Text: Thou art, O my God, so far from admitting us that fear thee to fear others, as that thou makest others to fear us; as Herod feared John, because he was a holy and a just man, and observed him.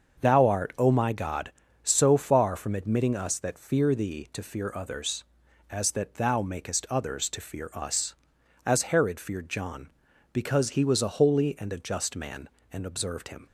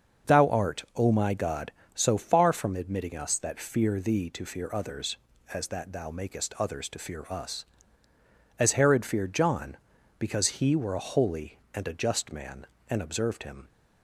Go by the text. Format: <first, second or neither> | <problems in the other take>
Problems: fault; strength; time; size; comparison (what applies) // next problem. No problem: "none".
first | starts louder than the rest; until 1.3 s; 6.5 dB; also in the first // says "were" for "was"; at 10.7 s